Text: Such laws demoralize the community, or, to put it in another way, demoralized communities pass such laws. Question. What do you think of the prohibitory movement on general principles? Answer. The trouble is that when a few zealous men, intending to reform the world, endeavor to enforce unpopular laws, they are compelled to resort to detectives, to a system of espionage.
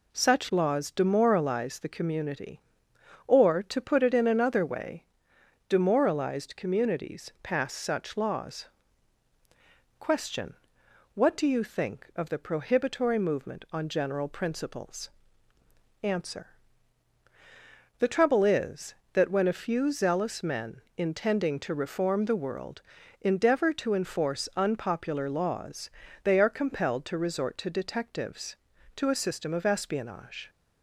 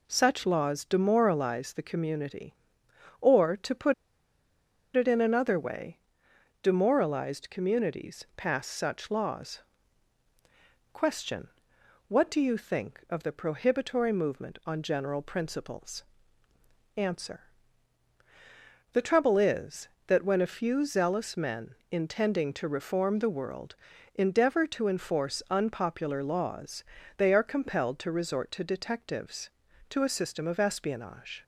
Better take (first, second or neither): first